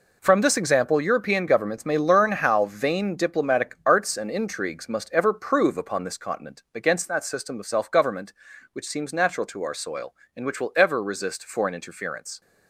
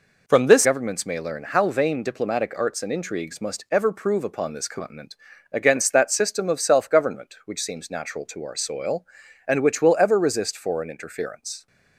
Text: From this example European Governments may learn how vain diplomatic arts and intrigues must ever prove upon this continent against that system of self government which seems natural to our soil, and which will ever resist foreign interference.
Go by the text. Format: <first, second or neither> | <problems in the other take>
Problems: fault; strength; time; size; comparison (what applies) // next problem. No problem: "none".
first | skips "example European"; at 0.6 s // pauses between "continent" and "against"; at 5.1 s; 0.38 s long